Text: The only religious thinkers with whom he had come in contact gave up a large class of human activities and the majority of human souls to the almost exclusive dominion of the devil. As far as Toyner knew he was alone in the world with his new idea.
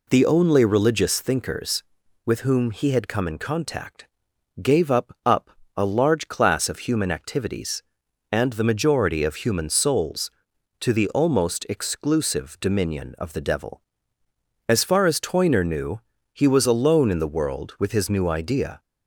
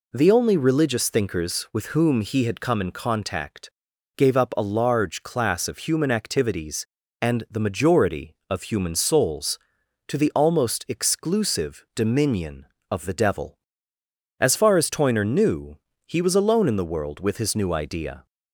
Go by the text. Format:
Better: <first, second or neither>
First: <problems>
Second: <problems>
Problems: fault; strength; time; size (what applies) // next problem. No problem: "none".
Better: second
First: pauses between "contact" and "gave"; noticeable; at 4.0 s; 0.54 s long // says "up" twice; at 5.2 s // pauses between "knew" and "he"; slight; at 15.9 s; 0.34 s long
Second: pauses between "contact" and "gave"; noticeable; at 3.6 s; 0.48 s long // pauses between "knew" and "he"; slight; at 15.7 s; 0.28 s long